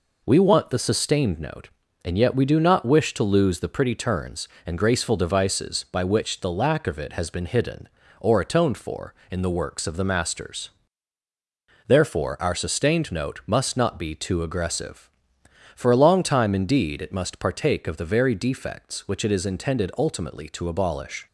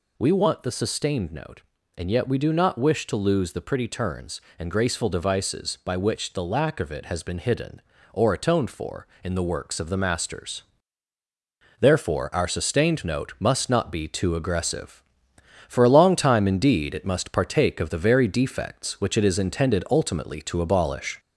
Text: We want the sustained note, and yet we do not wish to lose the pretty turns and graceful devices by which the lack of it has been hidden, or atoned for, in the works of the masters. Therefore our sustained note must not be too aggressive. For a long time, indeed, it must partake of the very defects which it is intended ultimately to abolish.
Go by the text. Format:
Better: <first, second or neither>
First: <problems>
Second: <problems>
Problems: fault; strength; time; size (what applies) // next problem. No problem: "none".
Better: first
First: none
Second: gets louder; slight; throughout; 2.5 dB